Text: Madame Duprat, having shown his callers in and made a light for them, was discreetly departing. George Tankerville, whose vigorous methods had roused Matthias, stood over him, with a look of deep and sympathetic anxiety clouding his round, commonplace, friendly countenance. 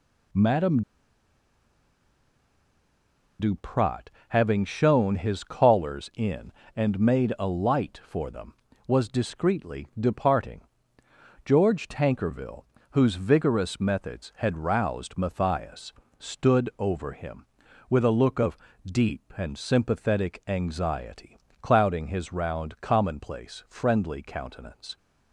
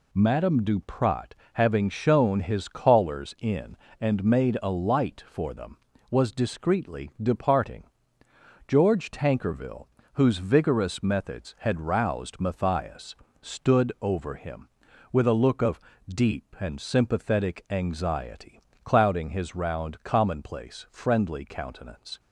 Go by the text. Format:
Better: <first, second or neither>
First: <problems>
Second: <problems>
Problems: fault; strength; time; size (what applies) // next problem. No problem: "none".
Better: second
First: pauses between "Madame" and "Duprat"; strong; at 0.8 s; 2.5 s long // pauses between "of" and "deep"; slight; at 18.5 s; 0.28 s long // pauses between "anxiety" and "clouding"; slight; at 21.3 s; 0.26 s long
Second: pauses between "of" and "deep"; slight; at 15.7 s; 0.28 s long // pauses between "anxiety" and "clouding"; slight; at 18.5 s; 0.26 s long